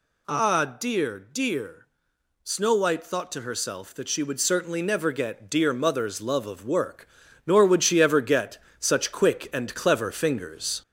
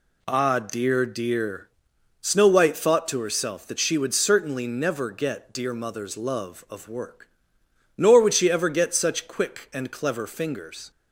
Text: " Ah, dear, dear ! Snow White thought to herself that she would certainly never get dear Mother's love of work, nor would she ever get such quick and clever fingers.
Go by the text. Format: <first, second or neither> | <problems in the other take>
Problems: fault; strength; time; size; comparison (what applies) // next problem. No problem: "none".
second | gets louder; slight; throughout; 3.5 dB // pauses between "get" and "such"; slight; at 8.5 s; 0.22 s long